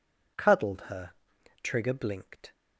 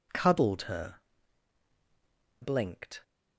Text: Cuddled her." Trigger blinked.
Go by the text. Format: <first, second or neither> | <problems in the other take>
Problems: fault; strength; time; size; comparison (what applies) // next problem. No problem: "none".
first | skips "Trigger"; at 1.7 s